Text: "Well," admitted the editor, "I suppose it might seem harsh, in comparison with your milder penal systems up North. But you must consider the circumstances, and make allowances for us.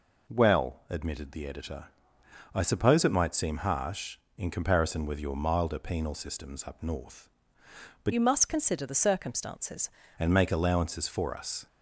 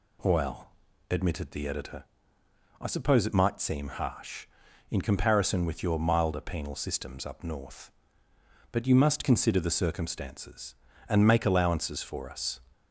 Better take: second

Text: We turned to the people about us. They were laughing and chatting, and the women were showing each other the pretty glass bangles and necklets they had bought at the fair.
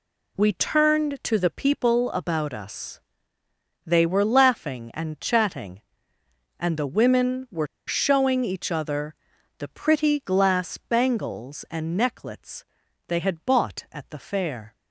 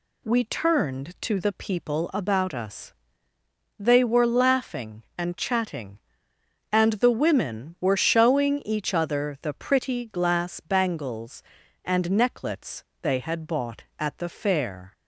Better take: second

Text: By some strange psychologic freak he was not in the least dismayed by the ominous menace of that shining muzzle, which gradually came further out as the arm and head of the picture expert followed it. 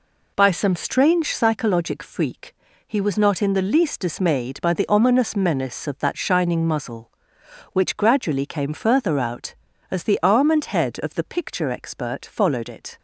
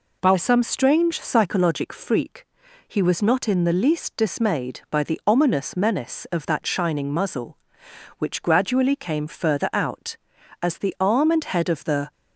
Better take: first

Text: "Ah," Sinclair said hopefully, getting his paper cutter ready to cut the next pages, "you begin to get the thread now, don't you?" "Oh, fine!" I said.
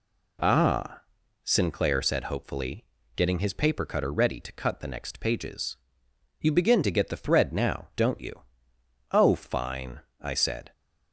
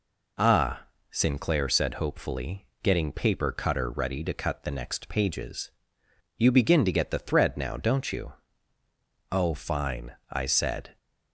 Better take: first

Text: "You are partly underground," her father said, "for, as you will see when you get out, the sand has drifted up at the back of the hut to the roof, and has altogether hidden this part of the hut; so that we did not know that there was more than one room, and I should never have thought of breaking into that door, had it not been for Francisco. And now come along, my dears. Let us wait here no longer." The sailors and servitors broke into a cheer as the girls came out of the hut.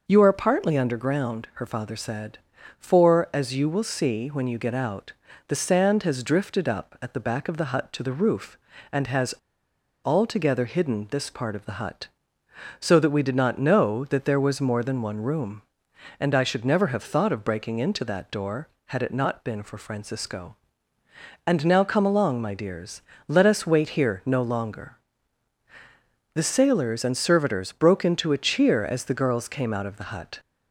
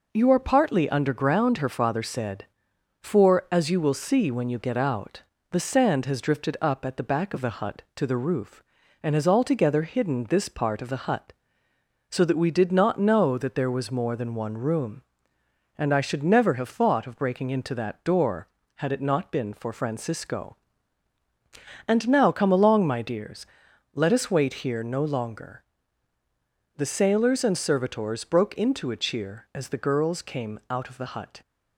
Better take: second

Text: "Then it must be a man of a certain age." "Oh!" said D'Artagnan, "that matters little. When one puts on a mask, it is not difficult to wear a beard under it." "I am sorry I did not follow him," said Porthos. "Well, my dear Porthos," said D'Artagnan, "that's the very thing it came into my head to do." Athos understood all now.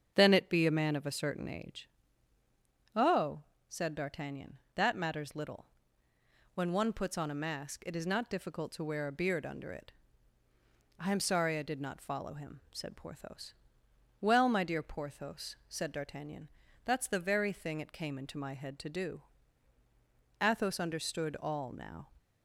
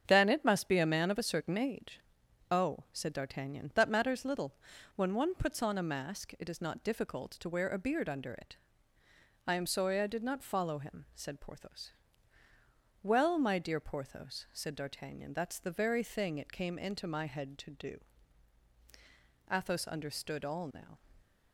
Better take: second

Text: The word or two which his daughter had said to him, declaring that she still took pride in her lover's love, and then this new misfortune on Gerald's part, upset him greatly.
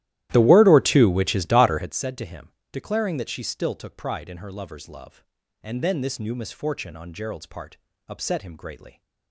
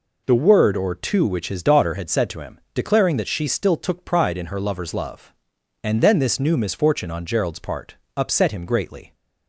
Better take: second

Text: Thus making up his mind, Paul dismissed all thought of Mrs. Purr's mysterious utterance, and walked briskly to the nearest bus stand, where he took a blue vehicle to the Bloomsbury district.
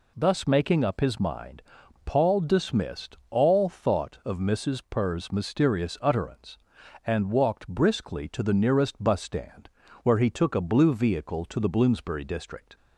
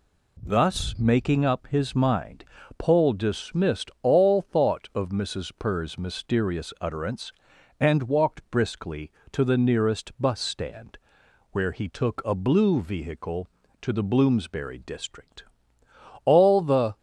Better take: first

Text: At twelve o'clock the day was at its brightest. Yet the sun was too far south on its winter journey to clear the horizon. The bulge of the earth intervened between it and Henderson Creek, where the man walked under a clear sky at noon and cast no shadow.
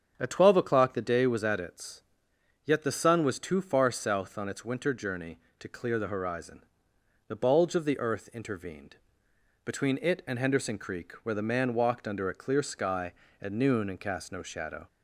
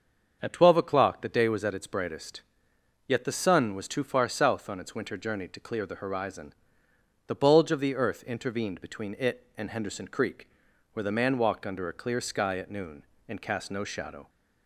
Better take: second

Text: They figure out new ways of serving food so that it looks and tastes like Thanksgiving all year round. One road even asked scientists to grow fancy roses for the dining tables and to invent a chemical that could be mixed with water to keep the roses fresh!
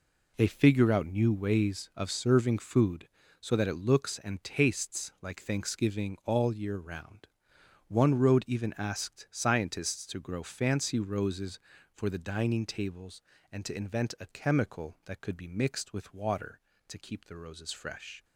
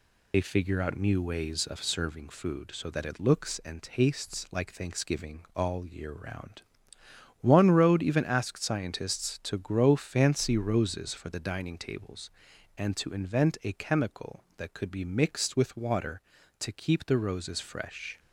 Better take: first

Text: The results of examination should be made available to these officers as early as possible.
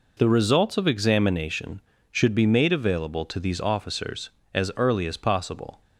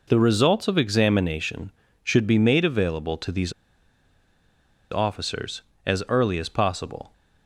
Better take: first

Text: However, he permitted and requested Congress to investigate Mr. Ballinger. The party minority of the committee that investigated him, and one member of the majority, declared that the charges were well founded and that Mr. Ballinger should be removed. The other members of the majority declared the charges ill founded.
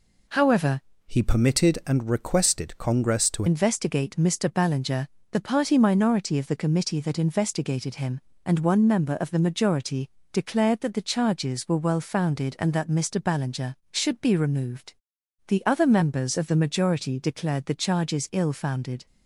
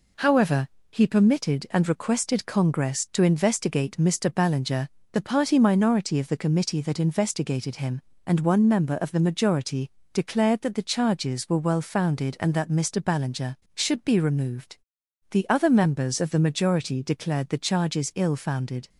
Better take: second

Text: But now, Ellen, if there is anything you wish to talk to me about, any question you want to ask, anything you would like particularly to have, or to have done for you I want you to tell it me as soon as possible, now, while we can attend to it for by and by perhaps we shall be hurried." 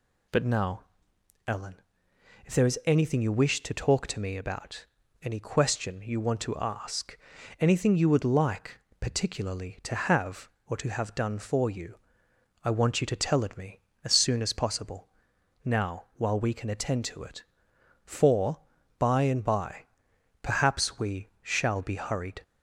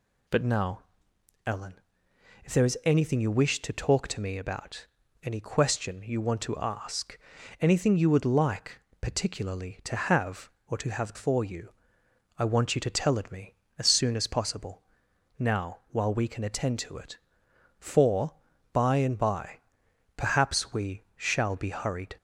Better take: first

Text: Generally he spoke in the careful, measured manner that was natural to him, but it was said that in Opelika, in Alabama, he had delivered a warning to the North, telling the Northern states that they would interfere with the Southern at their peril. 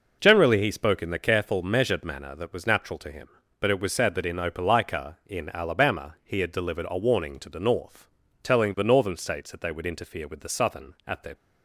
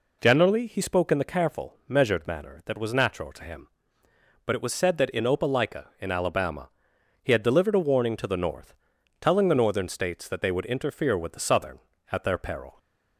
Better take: second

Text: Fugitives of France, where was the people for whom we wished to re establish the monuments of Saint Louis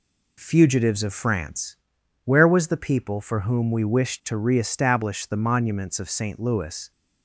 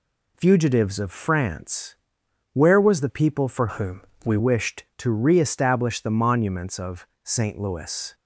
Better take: first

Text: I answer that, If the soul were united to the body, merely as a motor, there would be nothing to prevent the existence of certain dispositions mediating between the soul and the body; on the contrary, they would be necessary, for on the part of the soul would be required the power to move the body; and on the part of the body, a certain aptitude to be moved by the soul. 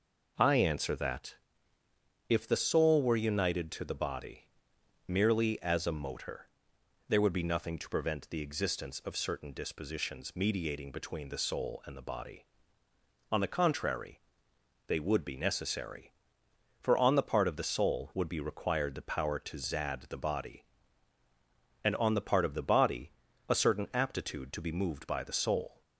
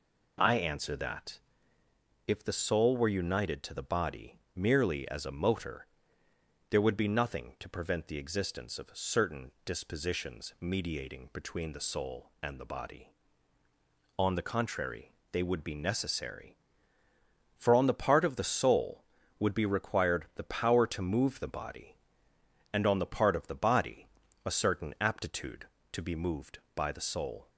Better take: second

